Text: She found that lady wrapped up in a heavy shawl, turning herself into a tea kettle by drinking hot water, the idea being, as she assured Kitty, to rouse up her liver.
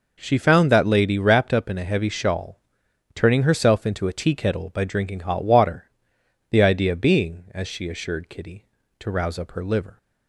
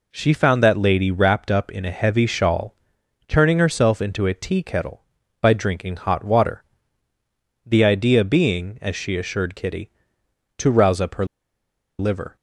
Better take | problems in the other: first | pauses between "her" and "liver"; noticeable; at 11.2 s; 0.73 s long

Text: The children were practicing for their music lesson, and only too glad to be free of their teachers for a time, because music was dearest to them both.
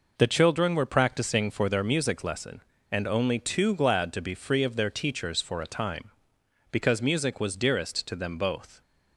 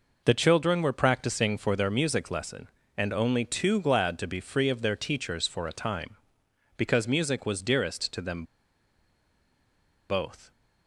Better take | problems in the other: first | pauses between "them" and "both"; strong; at 8.4 s; 1.6 s long

